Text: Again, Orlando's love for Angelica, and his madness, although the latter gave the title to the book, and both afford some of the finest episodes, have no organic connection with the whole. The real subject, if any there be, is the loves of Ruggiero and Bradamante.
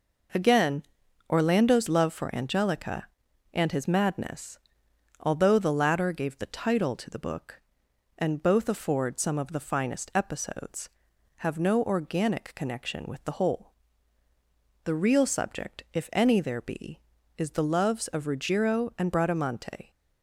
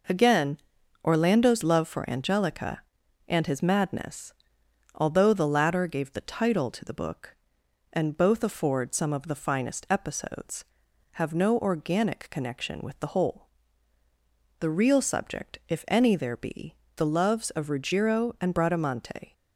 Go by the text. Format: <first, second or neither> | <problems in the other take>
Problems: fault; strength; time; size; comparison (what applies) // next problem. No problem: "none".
first | skips "is"; at 16.8 s